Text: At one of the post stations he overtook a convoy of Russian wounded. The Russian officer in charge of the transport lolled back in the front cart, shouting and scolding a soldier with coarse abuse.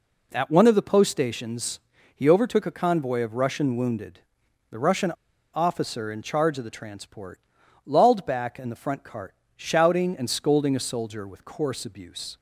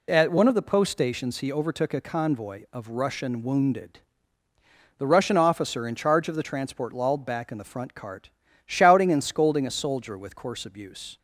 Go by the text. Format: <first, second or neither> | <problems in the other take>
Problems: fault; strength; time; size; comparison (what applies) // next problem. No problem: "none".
second | pauses between "stations" and "he"; slight; at 1.7 s; 0.34 s long // pauses between "Russian" and "officer"; at 5.1 s; 0.41 s long // pauses between "transport" and "lolled"; noticeable; at 7.3 s; 0.46 s long